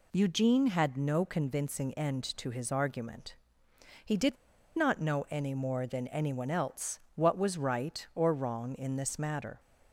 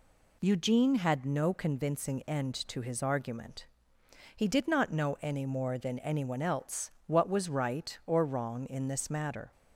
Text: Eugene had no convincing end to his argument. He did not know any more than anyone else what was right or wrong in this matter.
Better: second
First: pauses between "did" and "not"; at 4.3 s; 0.39 s long // pauses between "else" and "what"; slight; at 6.9 s; 0.16 s long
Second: pauses between "else" and "what"; slight; at 6.8 s; 0.16 s long

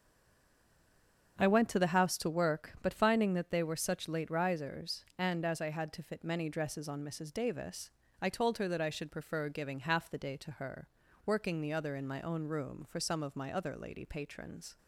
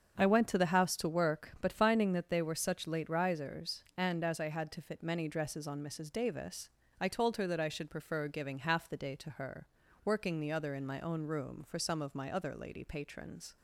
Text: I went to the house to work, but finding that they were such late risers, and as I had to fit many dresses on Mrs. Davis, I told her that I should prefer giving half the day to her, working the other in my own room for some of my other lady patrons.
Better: second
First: stays silent before the first word; noticeable; until 1.3 s; 1.3 s long // starts louder than the rest; strong; until 2.4 s; 7.5 dB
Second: starts louder than the rest; strong; until 1.2 s; 7.5 dB

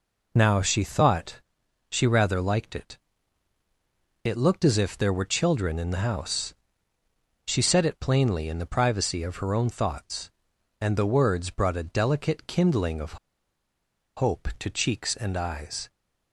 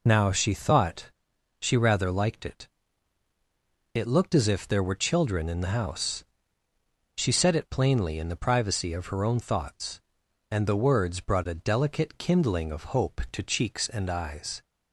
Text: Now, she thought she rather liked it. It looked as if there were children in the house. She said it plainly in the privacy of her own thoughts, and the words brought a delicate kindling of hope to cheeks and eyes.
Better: second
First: pauses between "thought" and "she"; noticeable; at 1.4 s; 0.48 s long // pauses between "of" and "hope"; at 13.1 s; 0.99 s long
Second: pauses between "thought" and "she"; noticeable; at 1.1 s; 0.48 s long

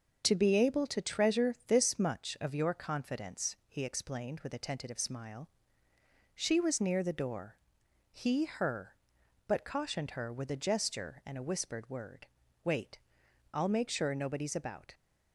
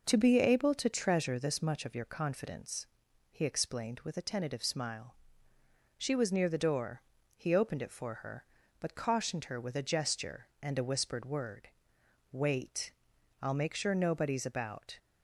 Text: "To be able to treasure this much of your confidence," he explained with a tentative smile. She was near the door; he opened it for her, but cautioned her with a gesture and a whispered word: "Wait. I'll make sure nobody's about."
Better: second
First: starts louder than the rest; until 1.2 s; 6 dB // skips "opened it for"; at 8.4 s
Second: none

